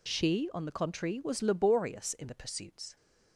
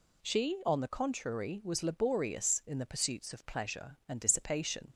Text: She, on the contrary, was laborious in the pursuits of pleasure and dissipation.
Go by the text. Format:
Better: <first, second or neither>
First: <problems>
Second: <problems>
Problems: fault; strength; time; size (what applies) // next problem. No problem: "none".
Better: second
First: stops before "of pleasure and dissipation"; at 2.9 s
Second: none